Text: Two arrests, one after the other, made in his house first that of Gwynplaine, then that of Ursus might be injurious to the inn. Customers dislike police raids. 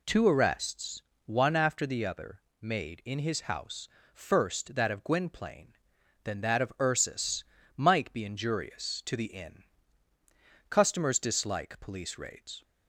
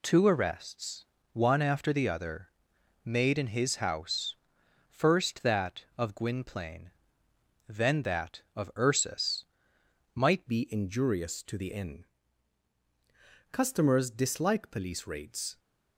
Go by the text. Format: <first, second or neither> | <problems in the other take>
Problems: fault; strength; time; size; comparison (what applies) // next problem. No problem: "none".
first | pauses between "house" and "first"; noticeable; at 4.3 s; 0.56 s long; slight in the first // pauses between "Ursus" and "might"; noticeable; at 9.4 s; 0.70 s long; slight in the first // changes voice at "be"; from 10.4 s on; 5.1 s long